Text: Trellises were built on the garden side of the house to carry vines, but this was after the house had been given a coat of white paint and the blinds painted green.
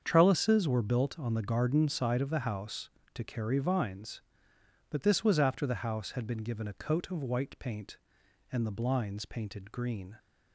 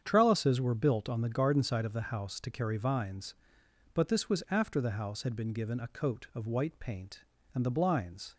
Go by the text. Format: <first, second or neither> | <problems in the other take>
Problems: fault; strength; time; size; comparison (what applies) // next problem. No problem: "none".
first | starts louder than the rest; strong; until 1.0 s; 8 dB; strong in the first // stops before "painted green"; at 8.3 s